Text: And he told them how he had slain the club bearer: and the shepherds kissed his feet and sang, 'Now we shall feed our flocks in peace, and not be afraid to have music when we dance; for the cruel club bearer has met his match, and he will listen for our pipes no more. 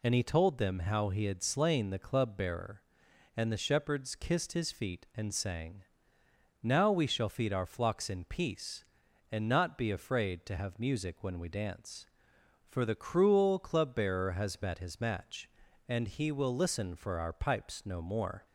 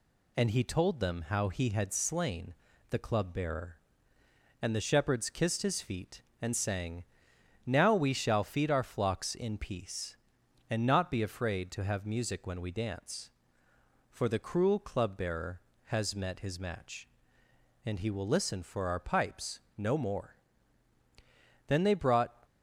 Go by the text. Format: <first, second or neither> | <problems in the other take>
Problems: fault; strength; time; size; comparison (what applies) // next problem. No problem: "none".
first | pauses between "slain" and "the"; slight; at 2.5 s; 0.36 s long // pauses between "pipes" and "no"; slight; at 19.6 s; 0.16 s long // goes on to say "Then they brought"; noticeable; from 21.6 s on; 0.76 s long